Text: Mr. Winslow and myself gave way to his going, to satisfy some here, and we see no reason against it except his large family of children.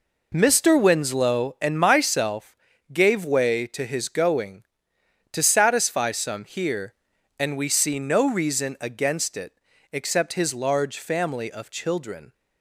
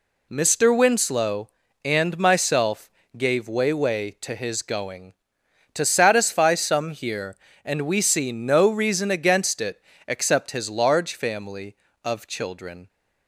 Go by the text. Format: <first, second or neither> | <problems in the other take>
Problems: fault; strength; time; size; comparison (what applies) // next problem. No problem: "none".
first | pauses between "myself" and "gave"; slight; at 2.9 s; 0.26 s long; slight in the first // says "way" twice; at 3.7 s // pauses between "it" and "except"; slight; at 9.8 s; 0.26 s long; slight in the first